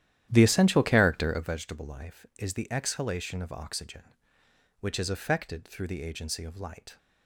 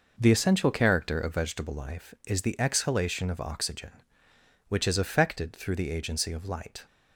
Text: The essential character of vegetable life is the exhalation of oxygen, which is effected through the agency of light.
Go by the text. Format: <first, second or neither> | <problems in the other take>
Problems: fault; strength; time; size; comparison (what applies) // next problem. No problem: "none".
second | starts louder than the rest; strong; until 1.6 s; 11.5 dB